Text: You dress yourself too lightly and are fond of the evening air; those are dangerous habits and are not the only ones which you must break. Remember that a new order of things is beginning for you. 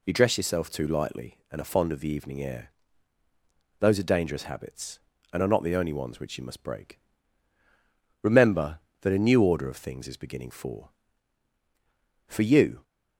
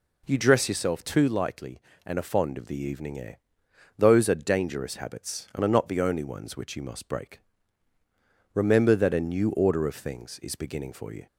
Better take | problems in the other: second | says "for" twice; at 12.2 s

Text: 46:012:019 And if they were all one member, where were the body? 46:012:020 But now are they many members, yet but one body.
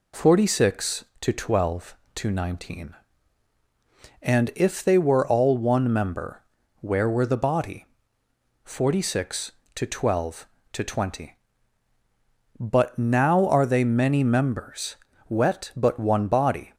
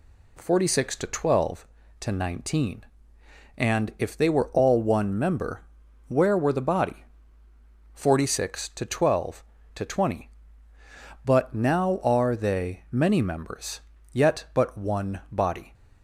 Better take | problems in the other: second | says "wet" for "yet"; at 15.2 s

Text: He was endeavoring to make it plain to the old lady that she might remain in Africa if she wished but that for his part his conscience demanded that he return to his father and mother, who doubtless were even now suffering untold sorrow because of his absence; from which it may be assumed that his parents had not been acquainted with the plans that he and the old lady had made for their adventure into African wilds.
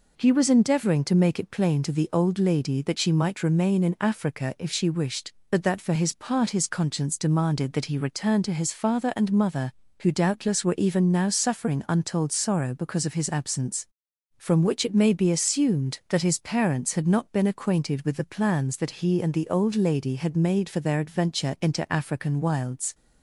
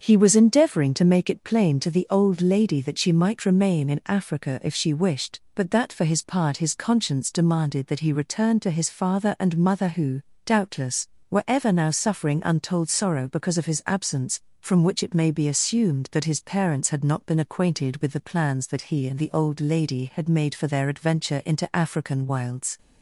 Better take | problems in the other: first | starts louder than the rest; until 1.0 s; 6.5 dB // pauses between "who" and "doubtless"; slight; at 10.2 s; 0.24 s long // says "ever" for "even"; at 11.4 s

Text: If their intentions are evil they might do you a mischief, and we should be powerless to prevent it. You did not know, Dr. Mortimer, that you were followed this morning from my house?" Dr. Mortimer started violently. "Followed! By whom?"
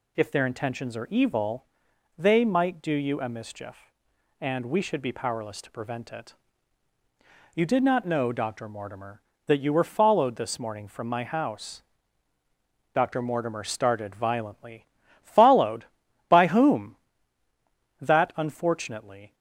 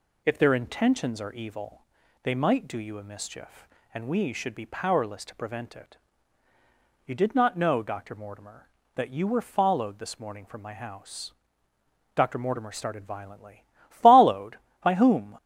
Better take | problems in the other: second | pauses between "evil" and "they"; noticeable; at 1.6 s; 0.52 s long; also in the second // goes on to say "That unfortunately"; from 18.0 s on; 1.3 s long

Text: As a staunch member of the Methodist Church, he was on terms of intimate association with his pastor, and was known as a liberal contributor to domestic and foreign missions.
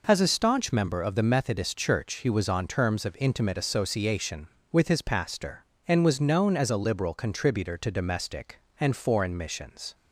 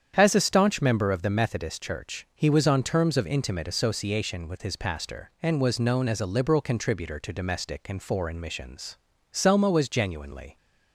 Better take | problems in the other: first | starts louder than the rest; strong; until 1.1 s; 8.5 dB // goes on to say "Selma was genuinely"; noticeable; from 9.3 s on; 1.2 s long

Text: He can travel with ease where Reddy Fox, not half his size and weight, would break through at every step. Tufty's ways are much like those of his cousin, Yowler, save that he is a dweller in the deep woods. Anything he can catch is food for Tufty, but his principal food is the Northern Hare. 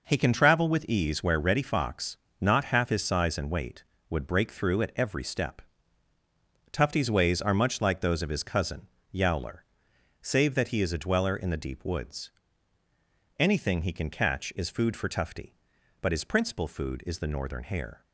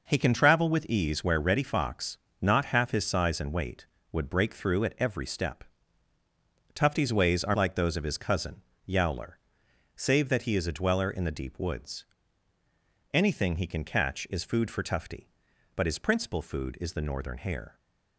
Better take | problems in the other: first | skips "much"; at 7.5 s

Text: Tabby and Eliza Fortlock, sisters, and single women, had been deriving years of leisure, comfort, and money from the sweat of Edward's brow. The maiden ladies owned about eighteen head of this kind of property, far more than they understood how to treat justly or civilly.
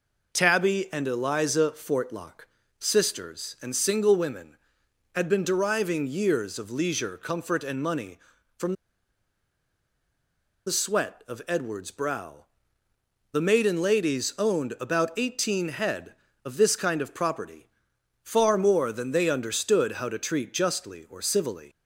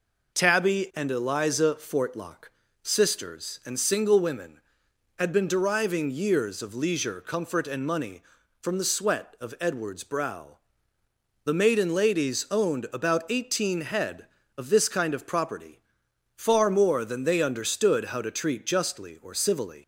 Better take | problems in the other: second | pauses between "from" and "the"; strong; at 8.7 s; 1.9 s long

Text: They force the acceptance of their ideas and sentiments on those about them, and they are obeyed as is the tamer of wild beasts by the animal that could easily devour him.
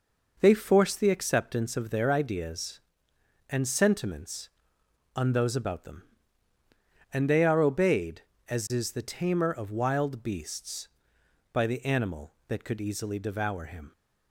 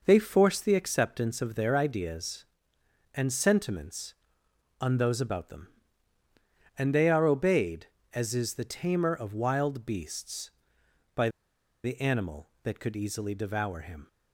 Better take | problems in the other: first | pauses between "by" and "the"; noticeable; at 11.2 s; 0.55 s long

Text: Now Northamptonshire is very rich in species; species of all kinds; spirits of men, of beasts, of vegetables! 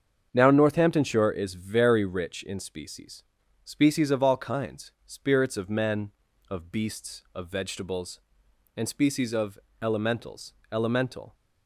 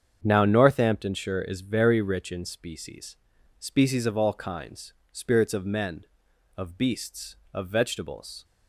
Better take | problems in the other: second | starts louder than the rest; strong; until 1.3 s; 7.5 dB; strong in the second // goes on to say "and species of elementals elemental"; strong; from 8.7 s on; 2.5 s long

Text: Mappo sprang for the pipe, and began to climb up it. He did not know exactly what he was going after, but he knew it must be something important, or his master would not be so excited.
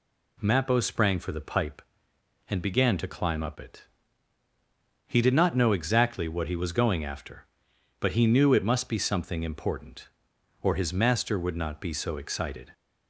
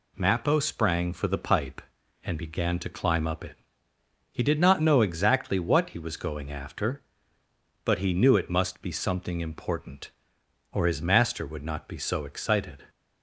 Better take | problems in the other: neither | none

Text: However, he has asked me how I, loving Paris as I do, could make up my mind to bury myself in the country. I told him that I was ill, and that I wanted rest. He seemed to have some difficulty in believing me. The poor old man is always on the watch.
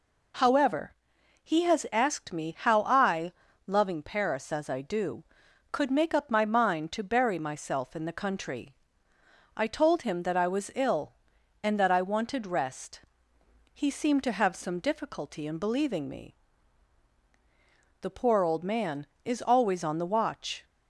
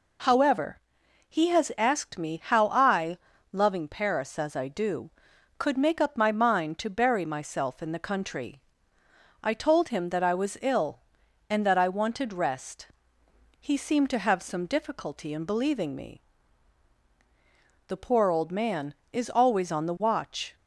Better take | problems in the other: neither | none

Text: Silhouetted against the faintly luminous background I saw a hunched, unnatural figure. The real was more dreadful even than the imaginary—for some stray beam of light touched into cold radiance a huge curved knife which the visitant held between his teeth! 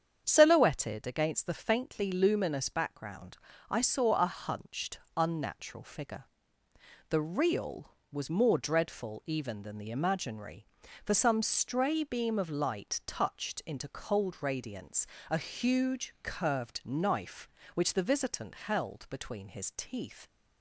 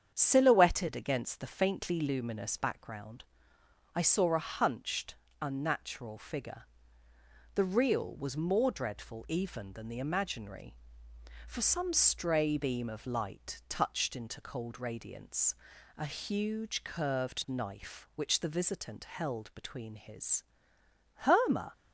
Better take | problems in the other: first | starts louder than the rest; strong; until 1.1 s; 8 dB; strong in the first // pauses between "background" and "I"; noticeable; at 3.2 s; 0.70 s long; slight in the first // pauses between "radiance" and "a"; at 15.5 s; 0.42 s long; slight in the first // says "herma" for "teeth"; at 21.2 s

